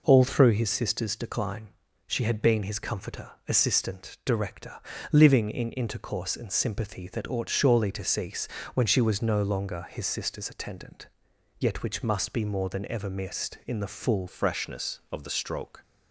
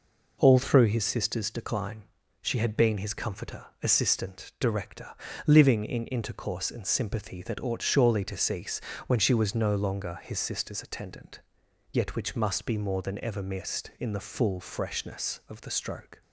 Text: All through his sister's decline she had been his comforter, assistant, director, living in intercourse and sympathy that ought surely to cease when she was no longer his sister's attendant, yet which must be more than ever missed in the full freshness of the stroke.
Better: second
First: pauses between "decline" and "she"; at 1.6 s; 0.38 s long // pauses between "cease" and "when"; slight; at 8.4 s; 0.28 s long // changes voice at "freshness"; from 14.2 s on; 1.6 s long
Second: pauses between "decline" and "she"; at 2.0 s; 0.38 s long // pauses between "cease" and "when"; slight; at 8.7 s; 0.28 s long

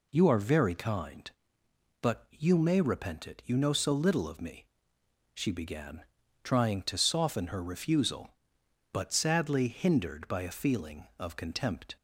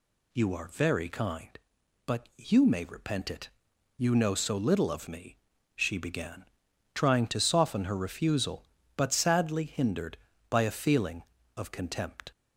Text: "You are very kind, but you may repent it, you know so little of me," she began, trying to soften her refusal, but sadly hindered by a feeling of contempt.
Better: neither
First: none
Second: none

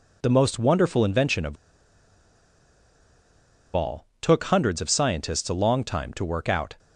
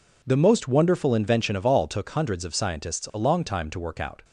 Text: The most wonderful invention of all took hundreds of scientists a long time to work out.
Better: second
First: pauses between "of" and "all"; strong; at 1.5 s; 2.2 s long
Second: none

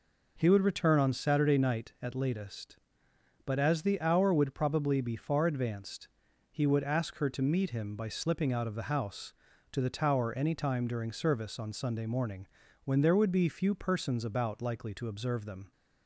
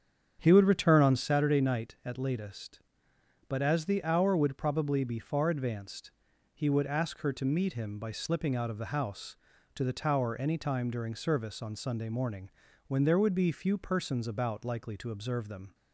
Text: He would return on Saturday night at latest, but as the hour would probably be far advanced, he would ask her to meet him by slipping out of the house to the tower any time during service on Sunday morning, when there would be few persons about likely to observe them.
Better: first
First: none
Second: starts louder than the rest; strong; until 1.4 s; 8 dB

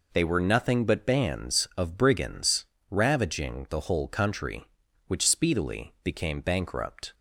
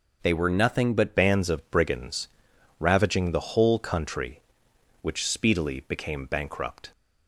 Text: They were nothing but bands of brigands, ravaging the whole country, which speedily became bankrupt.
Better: first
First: none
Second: changes voice at "bands"; from 1.1 s on; 5.8 s long

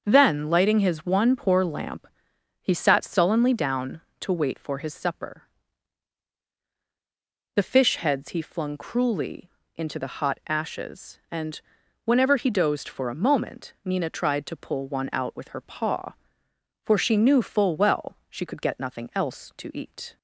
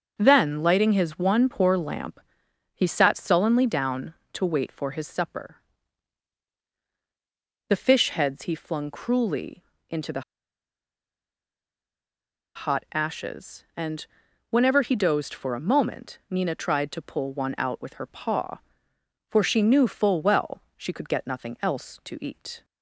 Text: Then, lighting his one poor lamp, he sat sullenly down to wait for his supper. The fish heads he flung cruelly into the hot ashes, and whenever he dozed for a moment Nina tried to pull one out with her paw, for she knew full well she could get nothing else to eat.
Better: first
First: starts louder than the rest; until 1.0 s; 6.5 dB // pauses between "cruelly" and "into"; slight; at 9.4 s; 0.26 s long // pauses between "and" and "whenever"; noticeable; at 11.5 s; 0.46 s long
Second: starts louder than the rest; until 1.1 s; 6.5 dB // pauses between "cruelly" and "into"; slight; at 9.6 s; 0.26 s long // pauses between "the" and "hot"; strong; at 10.2 s; 2.3 s long // pauses between "and" and "whenever"; noticeable; at 14.0 s; 0.46 s long // pauses between "well" and "she"; slight; at 20.6 s; 0.16 s long

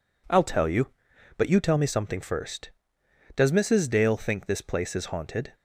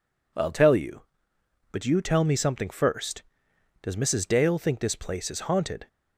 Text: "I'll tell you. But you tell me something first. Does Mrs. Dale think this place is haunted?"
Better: neither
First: none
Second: none

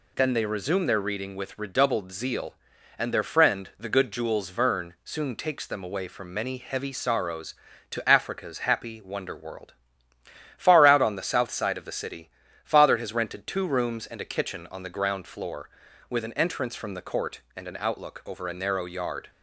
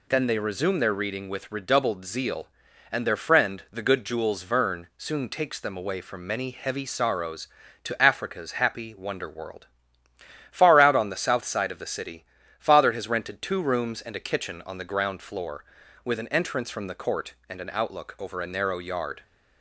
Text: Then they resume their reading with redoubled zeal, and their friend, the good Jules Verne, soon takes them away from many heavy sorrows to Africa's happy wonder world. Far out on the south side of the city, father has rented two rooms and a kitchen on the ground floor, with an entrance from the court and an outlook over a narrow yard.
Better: neither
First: none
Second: none

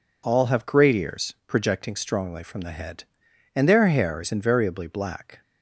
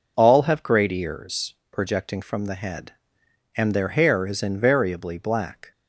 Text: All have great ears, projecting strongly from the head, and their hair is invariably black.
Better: first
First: none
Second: skips "strongly"; at 2.2 s

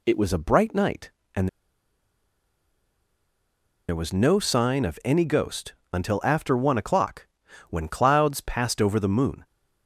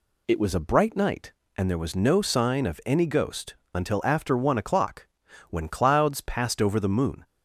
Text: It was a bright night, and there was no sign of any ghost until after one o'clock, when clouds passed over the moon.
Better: second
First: pauses between "and" and "there"; strong; at 1.4 s; 2.4 s long // pauses between "ghost" and "until"; slight; at 5.7 s; 0.18 s long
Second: pauses between "ghost" and "until"; slight; at 3.5 s; 0.18 s long

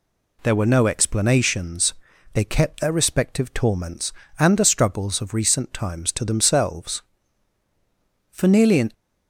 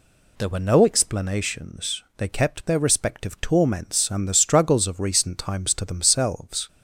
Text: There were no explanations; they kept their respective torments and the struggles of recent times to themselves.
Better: second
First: goes on to say "For nearly an"; noticeable; from 8.2 s on; 0.62 s long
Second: none

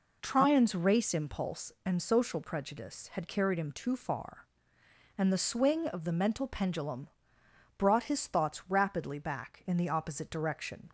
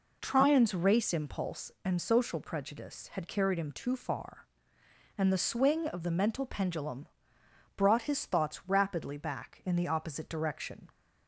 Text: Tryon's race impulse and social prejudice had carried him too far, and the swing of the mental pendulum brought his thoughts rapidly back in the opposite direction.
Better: neither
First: pauses between "pendulum" and "brought"; noticeable; at 7.0 s; 0.70 s long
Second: pauses between "pendulum" and "brought"; noticeable; at 7.0 s; 0.70 s long

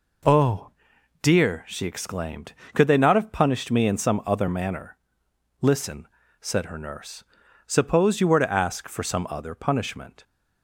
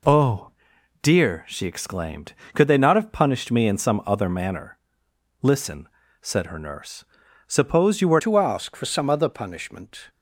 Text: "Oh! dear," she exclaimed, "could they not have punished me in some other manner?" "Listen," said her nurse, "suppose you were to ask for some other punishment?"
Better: first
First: none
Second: changes voice at "to"; from 8.1 s on; 1.9 s long

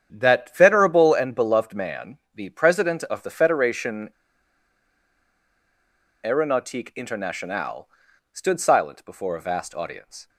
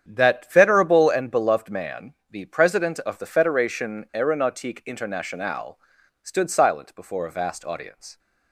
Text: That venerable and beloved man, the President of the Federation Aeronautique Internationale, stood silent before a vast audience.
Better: second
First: starts louder than the rest; strong; until 1.1 s; 8.5 dB // pauses between "Federation" and "Aeronautique"; strong; at 4.0 s; 2.1 s long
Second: starts louder than the rest; strong; until 1.0 s; 8.5 dB

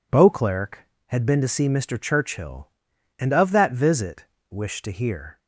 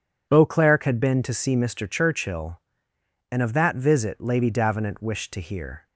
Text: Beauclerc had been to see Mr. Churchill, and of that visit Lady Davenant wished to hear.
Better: second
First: skips "Lady Davenant"; at 4.3 s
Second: none

